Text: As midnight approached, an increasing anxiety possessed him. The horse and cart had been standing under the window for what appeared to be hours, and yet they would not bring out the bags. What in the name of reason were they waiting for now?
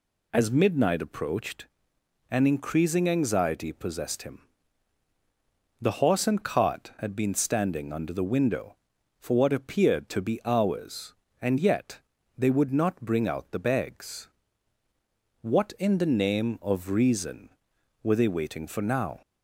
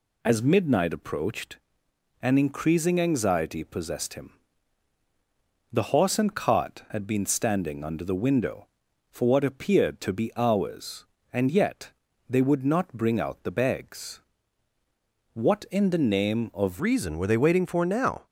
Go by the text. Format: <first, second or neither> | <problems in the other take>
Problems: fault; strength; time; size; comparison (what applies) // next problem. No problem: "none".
first | pauses between "yet" and "they"; at 11.8 s; 0.40 s long; also in the first // changes voice at "reason"; from 16.8 s on; 1.4 s long